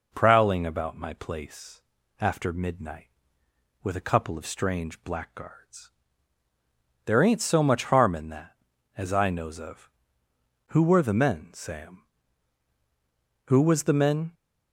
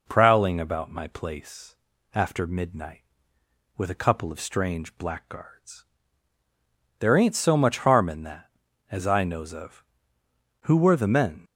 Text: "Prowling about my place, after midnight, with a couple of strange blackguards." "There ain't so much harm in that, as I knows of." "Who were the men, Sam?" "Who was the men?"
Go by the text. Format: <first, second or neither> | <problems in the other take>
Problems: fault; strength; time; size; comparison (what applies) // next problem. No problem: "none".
first | stops before "Sam Who was the men"; at 11.4 s